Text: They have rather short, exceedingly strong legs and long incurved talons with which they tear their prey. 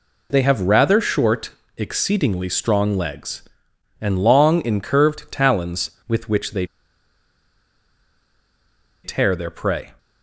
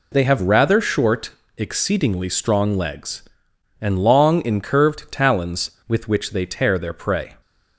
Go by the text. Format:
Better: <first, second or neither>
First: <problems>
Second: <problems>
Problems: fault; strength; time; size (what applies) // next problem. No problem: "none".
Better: second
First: pauses between "they" and "tear"; strong; at 6.6 s; 2.3 s long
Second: none